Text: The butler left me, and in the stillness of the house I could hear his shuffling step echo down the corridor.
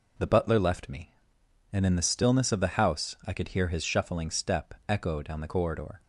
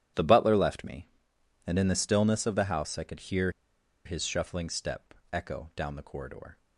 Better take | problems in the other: first | starts louder than the rest; strong; until 1.7 s; 11 dB // pauses between "hear" and "his"; noticeable; at 3.4 s; 0.55 s long // pauses between "step" and "echo"; slight; at 5.1 s; 0.18 s long

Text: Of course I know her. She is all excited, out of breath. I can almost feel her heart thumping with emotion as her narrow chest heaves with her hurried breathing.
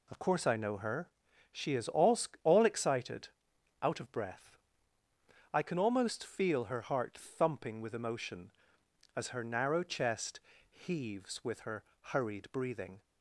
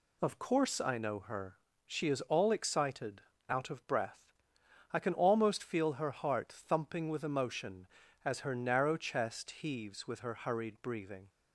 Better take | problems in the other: second | says "all" twice; at 2.4 s // pauses between "chest" and "heaves"; slight; at 10.3 s; 0.32 s long // pauses between "her" and "hurried"; slight; at 11.8 s; 0.30 s long

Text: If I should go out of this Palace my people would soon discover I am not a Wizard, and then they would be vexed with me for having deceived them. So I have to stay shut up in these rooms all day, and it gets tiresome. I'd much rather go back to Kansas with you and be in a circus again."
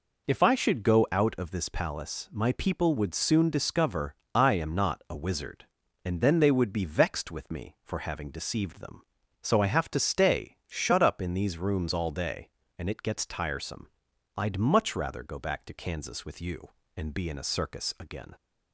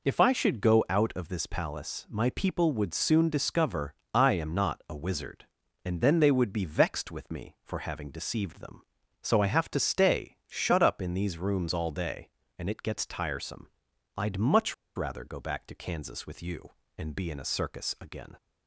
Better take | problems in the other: first | pauses between "discover" and "I"; slight; at 3.9 s; 0.20 s long; slight in the first // pauses between "much" and "rather"; slight; at 14.7 s; 0.23 s long

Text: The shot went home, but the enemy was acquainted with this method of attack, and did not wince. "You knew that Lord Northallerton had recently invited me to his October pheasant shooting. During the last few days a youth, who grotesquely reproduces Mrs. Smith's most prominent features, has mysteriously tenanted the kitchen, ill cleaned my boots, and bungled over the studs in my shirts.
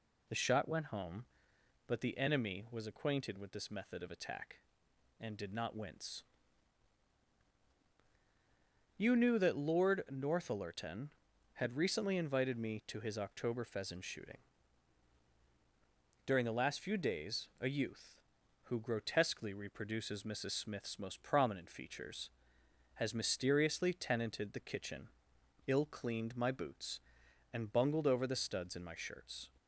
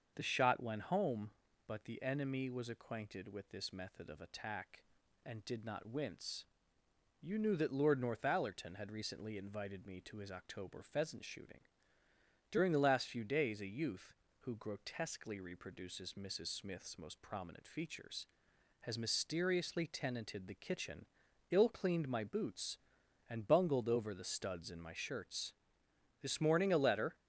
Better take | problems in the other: first | starts louder than the rest; until 1.1 s; 6.5 dB // goes on to say "This morning a letter"; noticeable; from 26.1 s on; 0.96 s long

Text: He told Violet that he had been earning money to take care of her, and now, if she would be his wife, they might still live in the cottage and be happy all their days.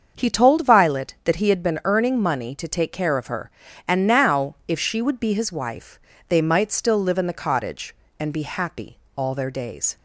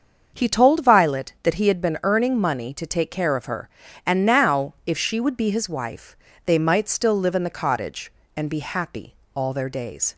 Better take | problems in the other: neither | starts louder than the rest; the same in both // pauses between "happy" and "all"; slight; the same in both

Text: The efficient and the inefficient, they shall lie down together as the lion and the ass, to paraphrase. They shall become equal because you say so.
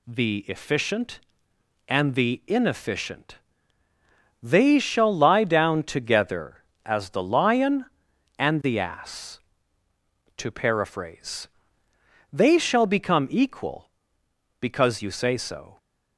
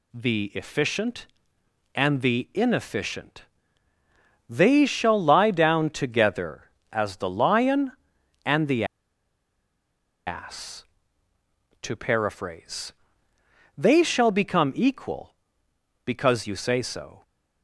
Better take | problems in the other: first | pauses between "the" and "ass"; strong; at 8.8 s; 1.4 s long

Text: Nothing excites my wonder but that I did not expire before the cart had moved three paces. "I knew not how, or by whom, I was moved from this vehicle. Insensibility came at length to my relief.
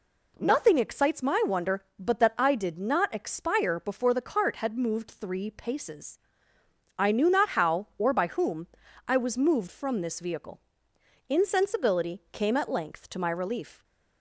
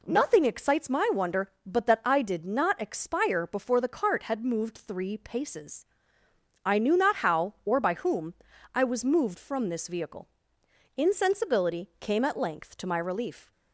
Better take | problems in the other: neither | none

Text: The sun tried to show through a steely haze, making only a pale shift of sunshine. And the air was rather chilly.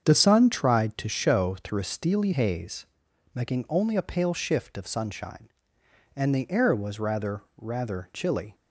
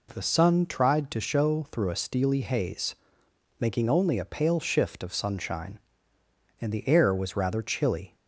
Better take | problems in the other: second | starts louder than the rest; strong; until 1.0 s; 7.5 dB // says "rather" twice; at 7.5 s

